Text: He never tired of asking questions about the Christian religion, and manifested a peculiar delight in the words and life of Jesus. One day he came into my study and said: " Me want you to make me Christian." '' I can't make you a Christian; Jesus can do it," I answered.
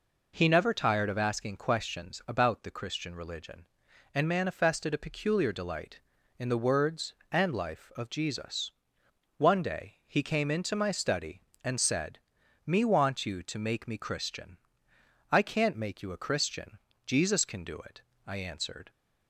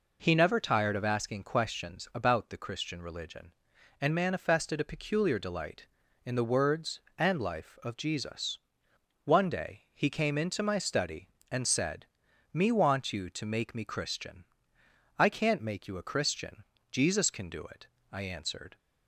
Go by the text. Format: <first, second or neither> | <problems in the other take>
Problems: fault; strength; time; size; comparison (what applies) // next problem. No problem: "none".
neither | none